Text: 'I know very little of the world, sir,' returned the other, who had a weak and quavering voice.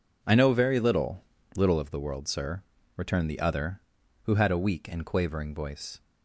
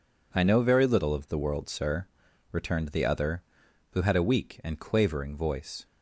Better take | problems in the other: second | says "little" twice; at 1.5 s

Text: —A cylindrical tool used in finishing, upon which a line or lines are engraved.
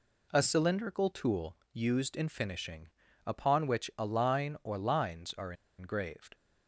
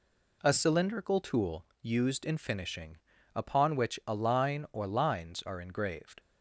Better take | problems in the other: second | pauses between "tool" and "used"; slight; at 1.5 s; 0.16 s long; slight in the second // pauses between "are" and "engraved"; slight; at 5.5 s; 0.25 s long

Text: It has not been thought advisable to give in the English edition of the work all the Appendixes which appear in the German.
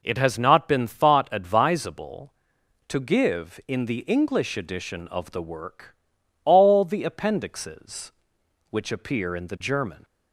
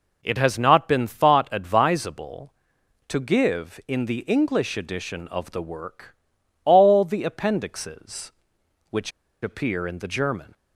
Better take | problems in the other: first | pauses between "work" and "all"; noticeable; at 6.1 s; 0.50 s long; noticeable in the first // pauses between "which" and "appear"; slight; at 9.1 s; 0.32 s long

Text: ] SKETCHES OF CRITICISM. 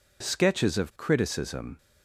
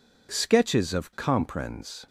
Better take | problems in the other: first | says "Comprens" for "CRITICISM"; at 1.1 s

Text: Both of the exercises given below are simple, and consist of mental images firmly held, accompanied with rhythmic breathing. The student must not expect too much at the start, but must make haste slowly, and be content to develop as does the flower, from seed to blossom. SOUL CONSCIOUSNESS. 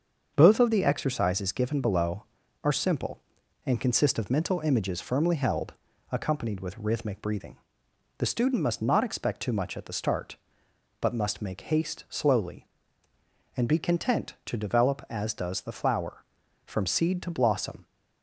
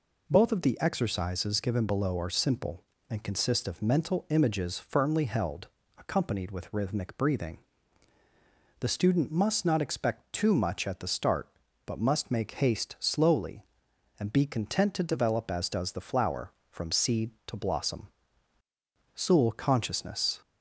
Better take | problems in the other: second | starts louder than the rest; until 1.3 s; 6.5 dB // stops before "SOUL CONSCIOUSNESS"; at 17.8 s

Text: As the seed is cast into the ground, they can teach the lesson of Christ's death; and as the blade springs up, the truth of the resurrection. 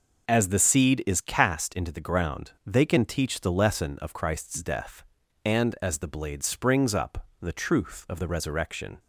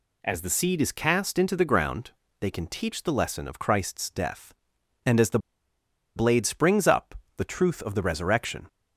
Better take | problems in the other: first | pauses between "the" and "blade"; noticeable; at 5.3 s; 0.78 s long

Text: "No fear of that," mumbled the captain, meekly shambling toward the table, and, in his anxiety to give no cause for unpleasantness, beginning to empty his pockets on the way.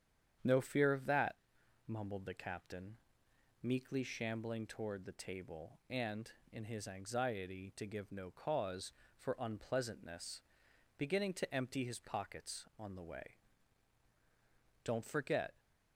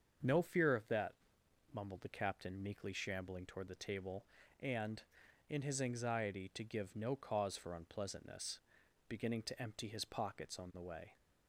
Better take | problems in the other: second | starts louder than the rest; strong; until 1.9 s; 8.5 dB; also in the second // goes on to say "Don't forget"; noticeable; from 14.8 s on; 0.74 s long

